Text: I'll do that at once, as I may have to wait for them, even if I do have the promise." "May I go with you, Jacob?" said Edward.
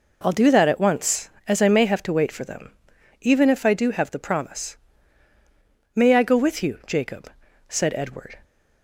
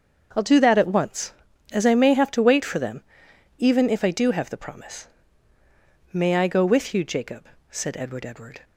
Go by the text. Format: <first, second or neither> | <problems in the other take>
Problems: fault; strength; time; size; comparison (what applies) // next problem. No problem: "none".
first | starts louder than the rest; until 1.3 s; 6.5 dB // says "Edward" twice; at 8.2 s